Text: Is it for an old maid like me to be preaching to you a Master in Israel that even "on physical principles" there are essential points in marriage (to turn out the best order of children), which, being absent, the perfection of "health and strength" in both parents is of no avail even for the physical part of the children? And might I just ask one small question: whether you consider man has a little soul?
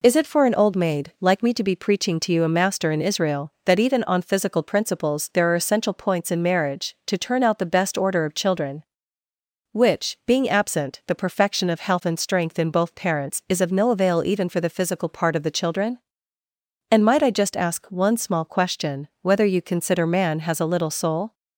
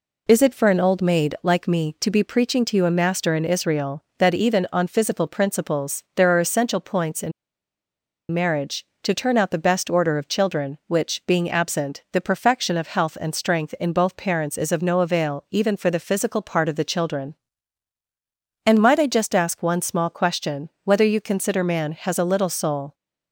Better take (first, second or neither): first